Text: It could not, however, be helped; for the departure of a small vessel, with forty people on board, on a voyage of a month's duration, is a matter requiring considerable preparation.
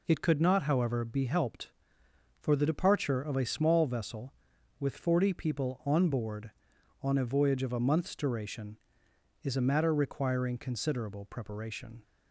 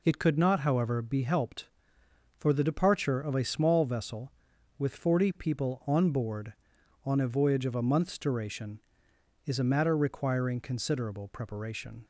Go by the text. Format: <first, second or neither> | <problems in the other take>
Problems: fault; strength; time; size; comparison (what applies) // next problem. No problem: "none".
neither | none